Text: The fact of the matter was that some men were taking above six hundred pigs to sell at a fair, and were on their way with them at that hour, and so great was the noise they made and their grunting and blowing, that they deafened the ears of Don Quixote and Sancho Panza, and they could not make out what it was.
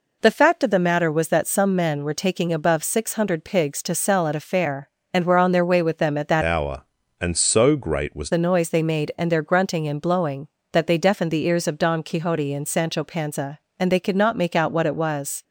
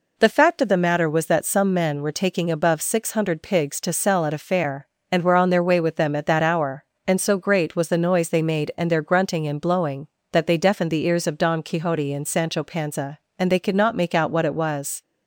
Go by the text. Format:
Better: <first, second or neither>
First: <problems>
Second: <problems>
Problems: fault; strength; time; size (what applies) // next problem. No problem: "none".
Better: second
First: changes voice from "hour" to "was"; from 6.4 to 8.2 s; 1.8 s long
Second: none